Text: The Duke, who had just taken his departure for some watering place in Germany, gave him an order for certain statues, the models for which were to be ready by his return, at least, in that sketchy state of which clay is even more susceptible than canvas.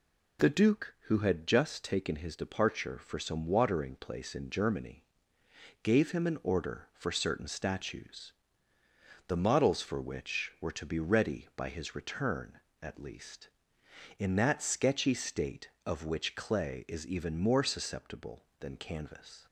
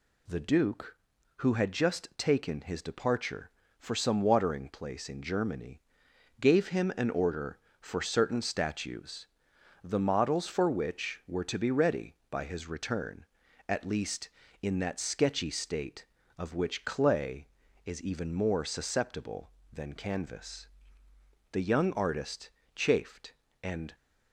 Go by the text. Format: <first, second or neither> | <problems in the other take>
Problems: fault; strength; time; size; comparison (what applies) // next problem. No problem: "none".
first | goes on to say "The young artist chafed and"; strong; from 21.5 s on; 2.4 s long